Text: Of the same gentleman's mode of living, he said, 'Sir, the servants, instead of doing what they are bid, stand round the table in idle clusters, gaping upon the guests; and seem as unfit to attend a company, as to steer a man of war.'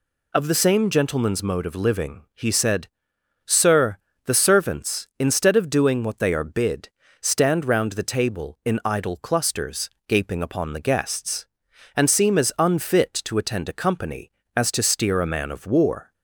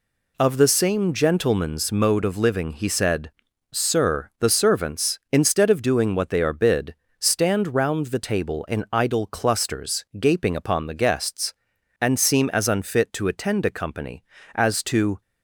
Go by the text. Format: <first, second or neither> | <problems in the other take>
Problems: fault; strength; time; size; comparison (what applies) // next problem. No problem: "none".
first | stops before "steer a man of war"; at 15.2 s